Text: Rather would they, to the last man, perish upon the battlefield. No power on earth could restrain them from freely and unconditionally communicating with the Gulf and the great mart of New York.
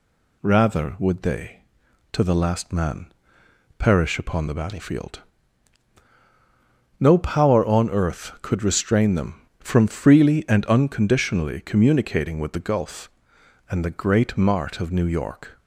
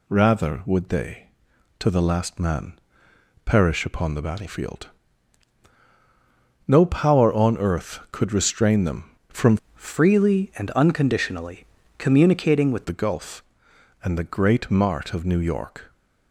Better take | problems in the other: first | changes voice from "freely" to "with"; from 9.7 to 12.8 s; 3.1 s long // pauses between "unconditionally" and "communicating"; slight; at 11.6 s; 0.32 s long

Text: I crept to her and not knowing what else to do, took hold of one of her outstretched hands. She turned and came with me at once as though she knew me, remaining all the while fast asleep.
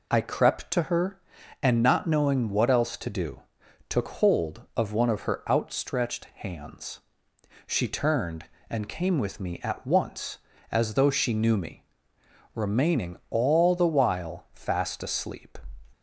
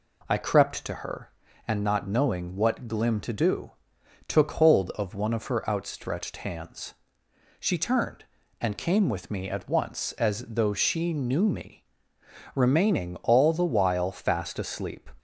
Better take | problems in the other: first | says "glim" for "else"; at 2.8 s

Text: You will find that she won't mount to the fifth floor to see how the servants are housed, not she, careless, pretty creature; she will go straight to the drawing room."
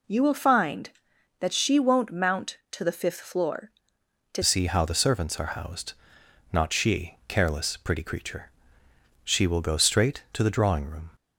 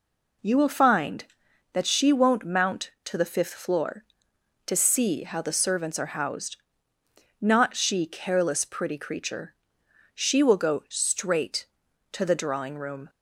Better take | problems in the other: second | changes voice at "see"; from 4.4 s on; 6.7 s long

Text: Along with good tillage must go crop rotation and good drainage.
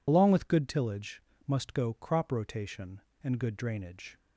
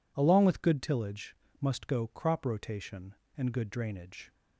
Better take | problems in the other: second | loses the start of "Along"; at 0.0 s; 65 ms // pauses between "tillage" and "must"; slight; at 1.2 s; 0.24 s long; slight in the second

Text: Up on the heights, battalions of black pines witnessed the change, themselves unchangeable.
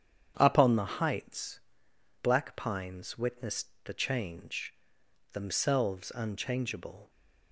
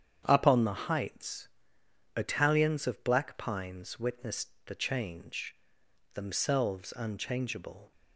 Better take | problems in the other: second | starts louder than the rest; strong; until 1.3 s; 8.5 dB; strong in the second // skips "battalions of"; at 1.9 s // pauses between "witnessed" and "the"; slight; at 3.6 s; 0.18 s long; slight in the second

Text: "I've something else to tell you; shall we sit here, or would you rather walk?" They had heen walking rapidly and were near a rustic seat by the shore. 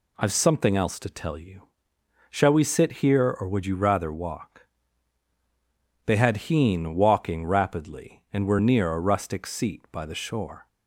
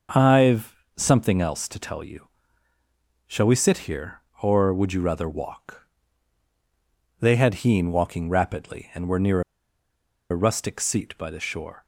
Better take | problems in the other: first | starts louder than the rest; until 1.3 s; 6 dB // pauses between "I've" and "something"; slight; at 0.7 s; 0.22 s long // pauses between "near" and "a"; noticeable; at 9.3 s; 0.90 s long

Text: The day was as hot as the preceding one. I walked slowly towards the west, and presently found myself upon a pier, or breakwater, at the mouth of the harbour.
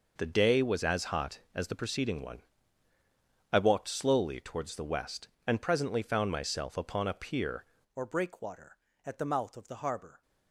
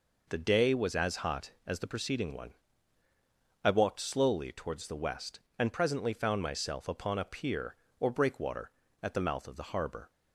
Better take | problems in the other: second | changes voice at "or"; from 7.9 s on; 2.3 s long

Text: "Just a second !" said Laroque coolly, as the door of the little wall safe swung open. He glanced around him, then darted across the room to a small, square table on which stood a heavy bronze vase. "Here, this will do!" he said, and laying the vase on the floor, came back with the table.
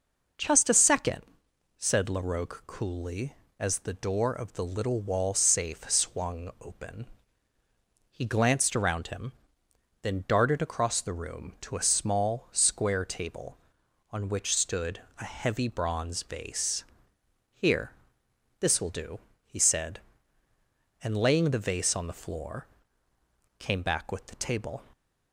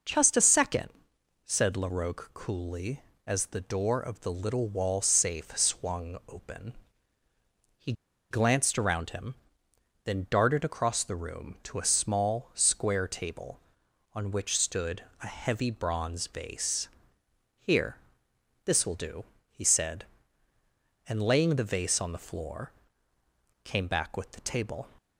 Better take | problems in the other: first | pauses between "He" and "glanced"; at 7.9 s; 0.38 s long // pauses between "stood" and "a"; slight; at 15.0 s; 0.18 s long; slight in the first

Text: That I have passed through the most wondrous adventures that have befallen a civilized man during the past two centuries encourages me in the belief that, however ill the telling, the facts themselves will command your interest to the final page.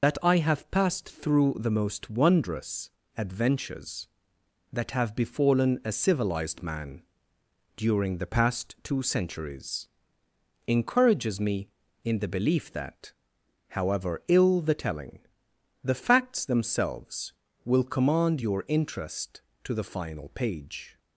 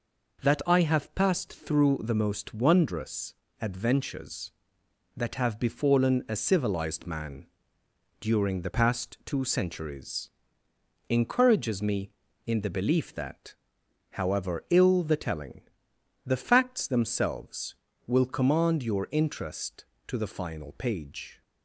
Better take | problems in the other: second | loses the start of "That"; at 0.0 s; 85 ms // pauses between "wondrous" and "adventures"; slight; at 2.8 s; 0.26 s long; slight in the second // pauses between "man" and "during"; noticeable; at 6.9 s; 0.78 s long; noticeable in the second // pauses between "centuries" and "encourages"; noticeable; at 9.8 s; 0.80 s long; noticeable in the second

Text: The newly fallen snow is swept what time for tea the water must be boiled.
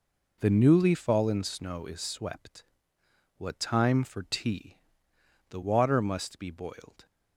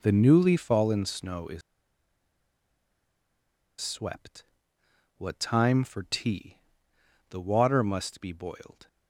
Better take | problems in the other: first | pauses between "is" and "swept"; strong; at 1.6 s; 2.2 s long // pauses between "swept" and "what"; noticeable; at 4.4 s; 0.72 s long; noticeable in the first // pauses between "tea" and "the"; noticeable; at 6.5 s; 0.70 s long; noticeable in the first

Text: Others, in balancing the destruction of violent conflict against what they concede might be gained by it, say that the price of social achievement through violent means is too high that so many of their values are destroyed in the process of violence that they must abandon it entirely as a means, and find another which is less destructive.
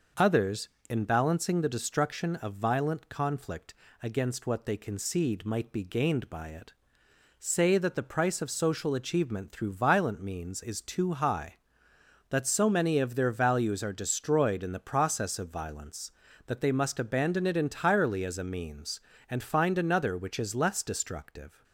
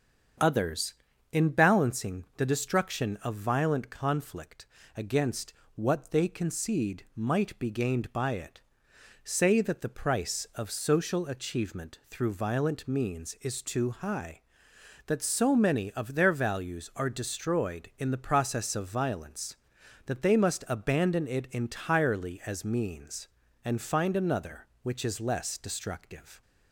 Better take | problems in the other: first | starts louder than the rest; strong; until 1.8 s; 7 dB // pauses between "conflict" and "against"; slight; at 4.6 s; 0.30 s long; slight in the first // pauses between "against" and "what"; slight; at 5.5 s; 0.22 s long // skips "a"; at 22.6 s

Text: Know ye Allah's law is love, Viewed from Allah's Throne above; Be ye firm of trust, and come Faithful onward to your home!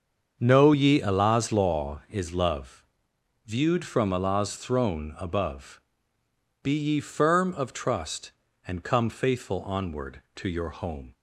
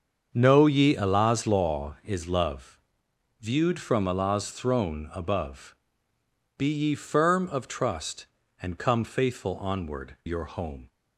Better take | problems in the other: first | starts louder than the rest; until 1.3 s; 7 dB; also in the first // skips "to"; at 10.2 s

